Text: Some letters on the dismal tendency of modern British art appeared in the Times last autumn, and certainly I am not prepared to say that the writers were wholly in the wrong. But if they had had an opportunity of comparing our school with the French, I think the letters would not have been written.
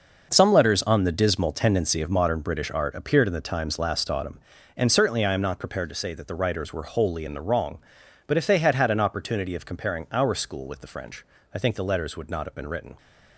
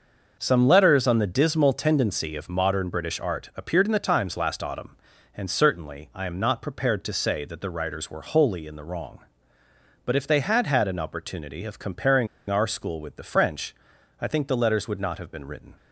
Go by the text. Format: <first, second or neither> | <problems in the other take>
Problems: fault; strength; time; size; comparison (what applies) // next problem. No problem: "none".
first | pauses between "comparing" and "our"; slight; at 12.2 s; 0.22 s long